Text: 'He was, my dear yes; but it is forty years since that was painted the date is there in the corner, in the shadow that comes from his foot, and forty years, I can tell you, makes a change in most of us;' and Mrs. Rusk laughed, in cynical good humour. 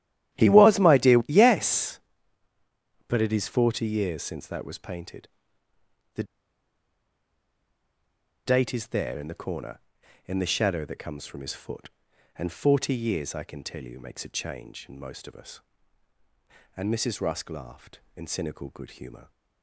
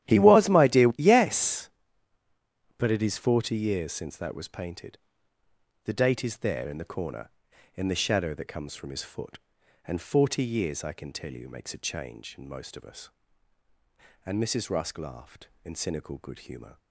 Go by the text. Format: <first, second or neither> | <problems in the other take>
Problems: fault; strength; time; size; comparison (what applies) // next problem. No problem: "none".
second | starts louder than the rest; strong; until 1.4 s; 12.5 dB; strong in the second // pauses between "painted" and "the"; noticeable; at 5.2 s; 0.86 s long; noticeable in the second // pauses between "the" and "date"; strong; at 6.2 s; 2.2 s long